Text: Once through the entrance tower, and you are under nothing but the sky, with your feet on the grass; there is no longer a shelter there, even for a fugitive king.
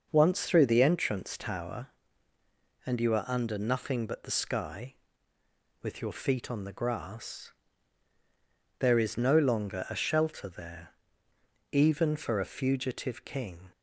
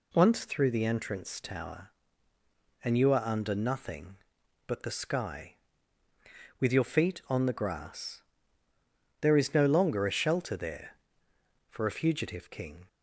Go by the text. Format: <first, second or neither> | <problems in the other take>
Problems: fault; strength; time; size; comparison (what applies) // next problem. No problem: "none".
first | skips "even"; at 11.3 s